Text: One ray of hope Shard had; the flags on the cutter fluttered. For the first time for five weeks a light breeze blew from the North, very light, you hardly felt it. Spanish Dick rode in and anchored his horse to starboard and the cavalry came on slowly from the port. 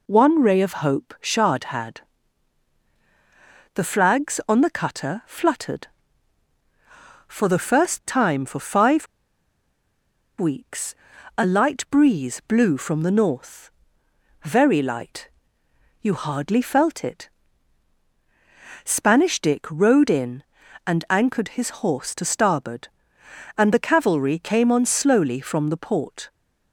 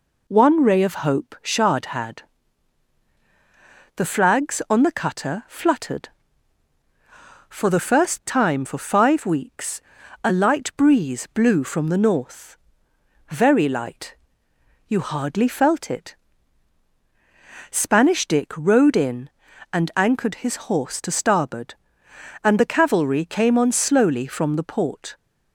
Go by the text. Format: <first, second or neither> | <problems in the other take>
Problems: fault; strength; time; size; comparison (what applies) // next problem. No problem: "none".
second | pauses between "five" and "weeks"; strong; at 9.0 s; 1.3 s long // pauses between "weeks" and "a"; at 10.9 s; 0.40 s long; also in the second